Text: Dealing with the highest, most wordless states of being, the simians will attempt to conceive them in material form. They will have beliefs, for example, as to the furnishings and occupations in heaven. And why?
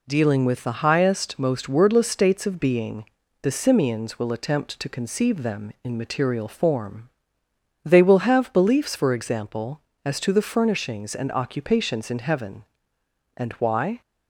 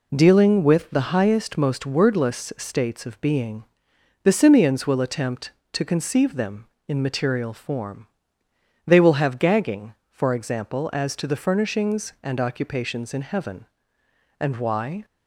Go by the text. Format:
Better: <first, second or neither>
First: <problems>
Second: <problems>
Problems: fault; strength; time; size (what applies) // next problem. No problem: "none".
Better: first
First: none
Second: says "gagging" for "beliefs"; at 9.3 s